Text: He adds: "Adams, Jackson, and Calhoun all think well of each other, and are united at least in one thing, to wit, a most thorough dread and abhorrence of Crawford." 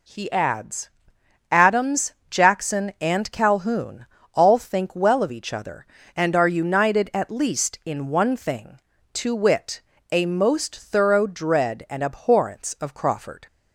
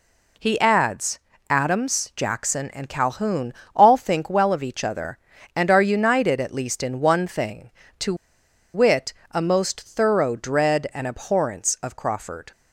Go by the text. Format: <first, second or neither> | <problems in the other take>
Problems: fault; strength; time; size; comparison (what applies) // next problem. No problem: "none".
first | pauses between "Calhoun" and "all"; slight; at 3.5 s; 0.20 s long; slight in the first // pauses between "to" and "wit"; noticeable; at 8.1 s; 0.60 s long